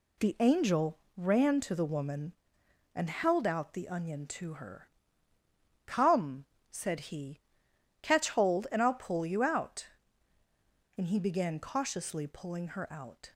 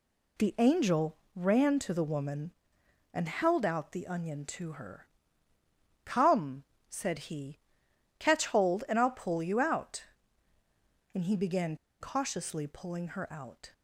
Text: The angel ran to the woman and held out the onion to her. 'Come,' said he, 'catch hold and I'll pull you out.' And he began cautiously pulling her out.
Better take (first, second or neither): first